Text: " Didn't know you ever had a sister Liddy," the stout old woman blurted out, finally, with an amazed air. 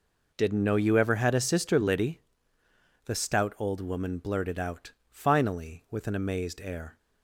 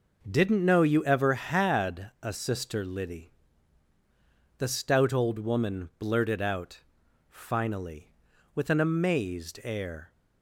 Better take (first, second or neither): neither